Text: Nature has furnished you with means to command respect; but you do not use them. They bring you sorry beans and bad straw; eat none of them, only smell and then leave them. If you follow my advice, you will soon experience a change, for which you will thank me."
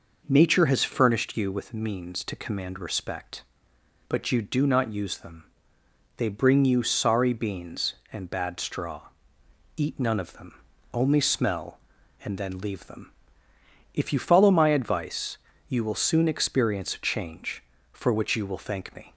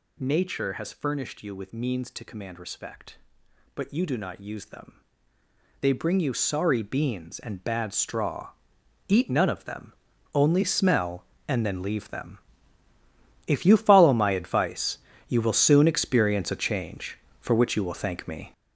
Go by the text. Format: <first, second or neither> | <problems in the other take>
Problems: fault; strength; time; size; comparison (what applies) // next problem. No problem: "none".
first | gets louder; strong; throughout; 8 dB